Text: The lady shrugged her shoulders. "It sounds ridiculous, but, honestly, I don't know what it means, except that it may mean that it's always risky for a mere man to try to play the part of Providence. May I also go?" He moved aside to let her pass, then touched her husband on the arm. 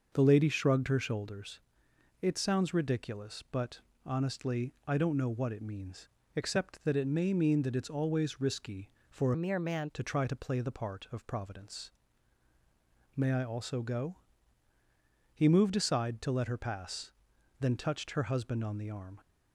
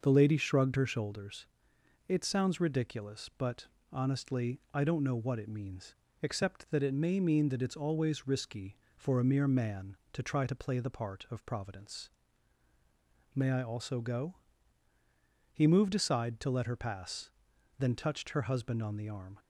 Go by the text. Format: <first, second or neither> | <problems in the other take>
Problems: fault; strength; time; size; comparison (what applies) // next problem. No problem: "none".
second | starts louder than the rest; noticeable; until 1.1 s; 6 dB // changes voice from "a" to "man"; from 9.3 to 9.8 s; 0.5 s long